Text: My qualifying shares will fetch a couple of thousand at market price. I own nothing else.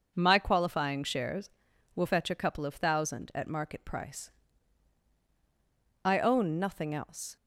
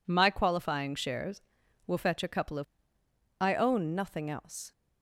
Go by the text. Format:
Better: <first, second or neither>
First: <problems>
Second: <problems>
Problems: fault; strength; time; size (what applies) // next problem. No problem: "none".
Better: first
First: none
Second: skips "thousand at market price"; at 3.0 s